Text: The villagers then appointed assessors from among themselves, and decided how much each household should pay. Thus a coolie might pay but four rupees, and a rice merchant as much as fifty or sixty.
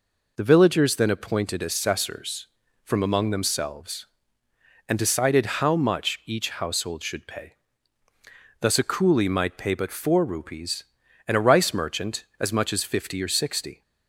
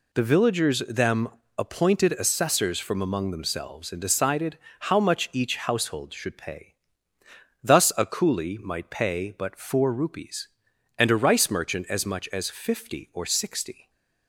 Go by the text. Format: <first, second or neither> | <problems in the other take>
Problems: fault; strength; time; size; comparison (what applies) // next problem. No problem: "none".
first | says "them" for "then"; at 0.7 s // pauses between "decided" and "how"; slight; at 4.5 s; 0.22 s long